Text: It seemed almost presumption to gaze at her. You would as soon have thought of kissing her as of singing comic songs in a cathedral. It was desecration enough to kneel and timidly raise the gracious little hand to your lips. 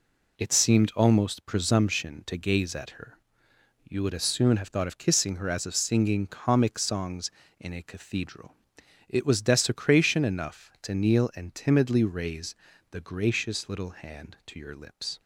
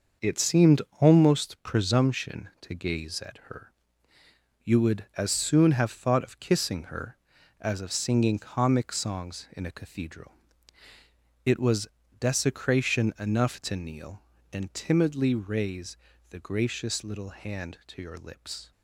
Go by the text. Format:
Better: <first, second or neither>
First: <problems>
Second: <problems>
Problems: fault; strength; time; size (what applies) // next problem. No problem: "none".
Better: first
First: pauses between "raise" and "the"; at 12.5 s; 0.38 s long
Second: starts louder than the rest; until 1.4 s; 6.5 dB // pauses between "seemed" and "almost"; slight; at 0.8 s; 0.20 s long // pauses between "was" and "desecration"; slight; at 11.8 s; 0.32 s long // pauses between "raise" and "the"; slight; at 15.9 s; 0.32 s long